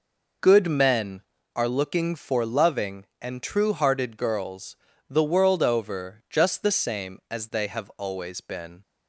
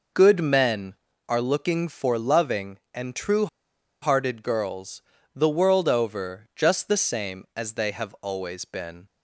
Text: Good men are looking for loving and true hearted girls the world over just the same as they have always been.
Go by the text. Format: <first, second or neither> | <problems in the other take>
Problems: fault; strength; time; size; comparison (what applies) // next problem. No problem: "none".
first | pauses between "true" and "hearted"; noticeable; at 3.4 s; 0.55 s long // pauses between "girls" and "the"; slight; at 5.0 s; 0.32 s long; slight in the first